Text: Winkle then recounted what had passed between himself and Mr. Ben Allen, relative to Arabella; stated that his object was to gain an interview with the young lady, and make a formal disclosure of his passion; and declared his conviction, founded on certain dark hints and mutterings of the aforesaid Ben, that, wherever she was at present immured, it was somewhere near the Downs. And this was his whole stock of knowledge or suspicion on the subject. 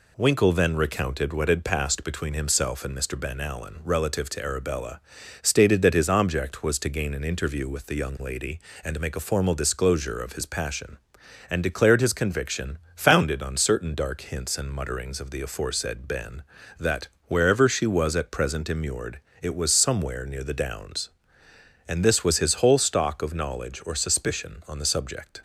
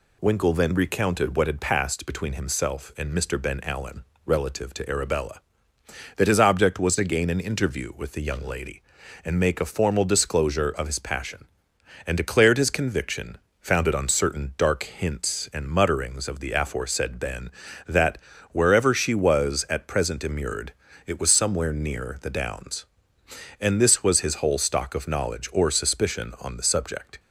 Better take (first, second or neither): first